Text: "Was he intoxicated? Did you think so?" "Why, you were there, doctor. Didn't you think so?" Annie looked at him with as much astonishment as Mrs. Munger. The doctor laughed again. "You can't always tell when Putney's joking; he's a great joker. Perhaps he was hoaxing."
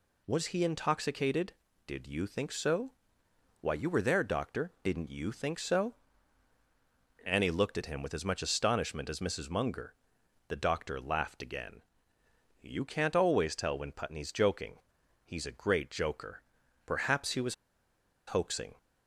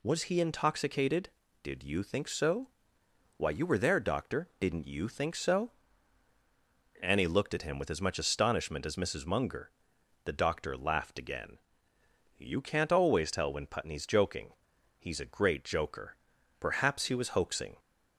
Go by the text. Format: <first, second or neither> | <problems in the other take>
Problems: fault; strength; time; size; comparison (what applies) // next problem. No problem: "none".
second | pauses between "was" and "hoaxing"; noticeable; at 17.5 s; 0.73 s long